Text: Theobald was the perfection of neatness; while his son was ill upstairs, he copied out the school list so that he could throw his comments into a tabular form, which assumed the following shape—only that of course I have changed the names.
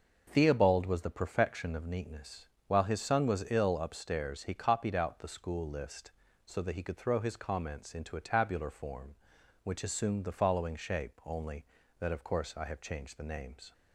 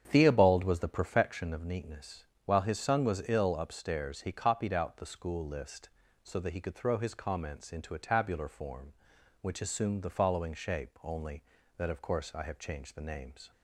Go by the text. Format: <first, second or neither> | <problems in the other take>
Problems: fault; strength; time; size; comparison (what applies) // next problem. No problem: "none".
first | starts louder than the rest; strong; until 1.3 s; 8 dB